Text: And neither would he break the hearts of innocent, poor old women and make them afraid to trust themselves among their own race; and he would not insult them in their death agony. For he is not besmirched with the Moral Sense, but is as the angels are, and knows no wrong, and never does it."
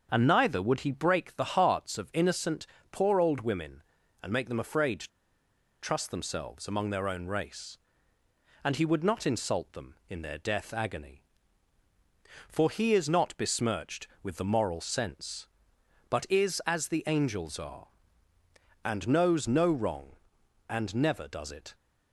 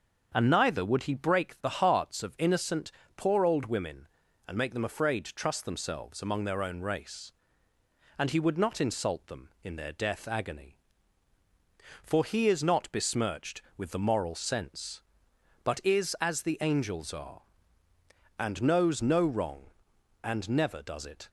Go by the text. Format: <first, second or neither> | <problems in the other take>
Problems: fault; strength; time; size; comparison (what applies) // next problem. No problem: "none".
second | starts louder than the rest; until 1.1 s; 6.5 dB; also in the second // pauses between "to" and "trust"; noticeable; at 5.0 s; 0.70 s long